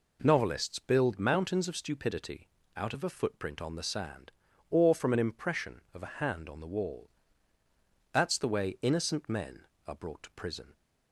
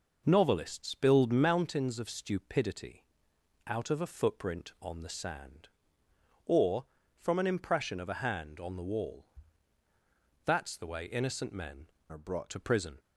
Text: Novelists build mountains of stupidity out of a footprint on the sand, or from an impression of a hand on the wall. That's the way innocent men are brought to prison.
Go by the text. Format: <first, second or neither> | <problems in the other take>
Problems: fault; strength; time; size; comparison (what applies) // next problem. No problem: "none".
first | pauses between "stupidity" and "out"; noticeable; at 3.0 s; 0.64 s long; slight in the first // changes voice from "are" to "brought"; from 12.0 to 12.4 s; 0.4 s long